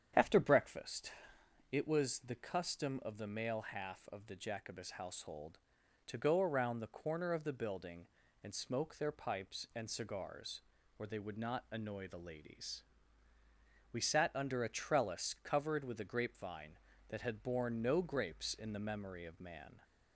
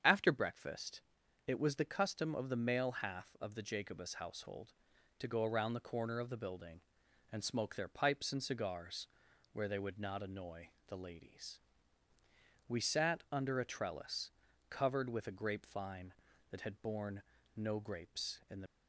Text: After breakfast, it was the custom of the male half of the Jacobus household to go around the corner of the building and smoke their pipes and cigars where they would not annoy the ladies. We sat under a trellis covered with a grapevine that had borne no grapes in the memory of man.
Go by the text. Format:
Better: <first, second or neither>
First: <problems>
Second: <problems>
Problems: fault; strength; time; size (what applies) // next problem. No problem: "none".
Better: first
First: starts louder than the rest; strong; until 1.7 s; 8.5 dB // pauses between "cigars" and "where"; at 10.6 s; 0.38 s long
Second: starts louder than the rest; strong; until 1.0 s; 8 dB // pauses between "cigars" and "where"; at 9.0 s; 0.44 s long // pauses between "annoy" and "the"; slight; at 10.6 s; 0.20 s long // pauses between "trellis" and "covered"; at 14.3 s; 0.40 s long // pauses between "borne" and "no"; slight; at 17.2 s; 0.34 s long // stops before "memory of man"; at 18.6 s